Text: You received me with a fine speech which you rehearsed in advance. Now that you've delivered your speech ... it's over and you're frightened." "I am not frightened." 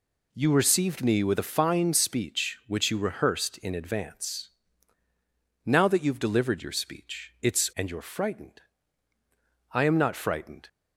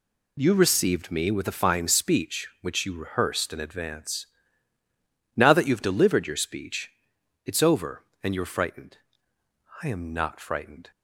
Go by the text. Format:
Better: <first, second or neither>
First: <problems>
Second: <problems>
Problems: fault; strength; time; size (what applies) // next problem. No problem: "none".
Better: second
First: skips "over"; at 7.7 s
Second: none